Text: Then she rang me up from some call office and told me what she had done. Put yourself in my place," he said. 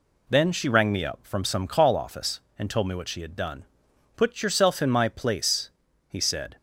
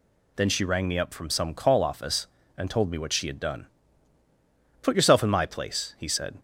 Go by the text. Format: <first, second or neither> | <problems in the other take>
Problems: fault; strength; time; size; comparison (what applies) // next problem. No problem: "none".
neither | none